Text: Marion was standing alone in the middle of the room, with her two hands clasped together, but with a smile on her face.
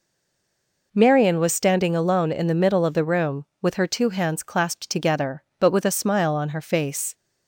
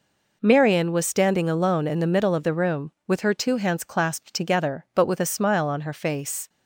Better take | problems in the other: second | stays silent before the first word; slight; until 0.9 s; 0.9 s long

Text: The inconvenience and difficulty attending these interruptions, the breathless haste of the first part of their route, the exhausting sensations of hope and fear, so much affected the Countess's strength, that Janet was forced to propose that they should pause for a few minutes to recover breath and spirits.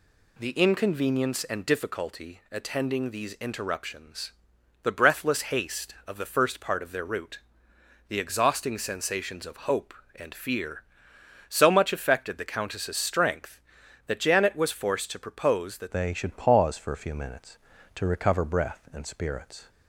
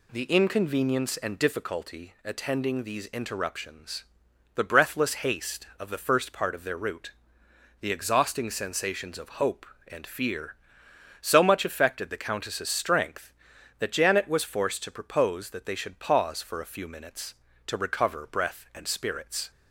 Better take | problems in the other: second | changes voice at "they"; from 15.9 s on; 3.7 s long

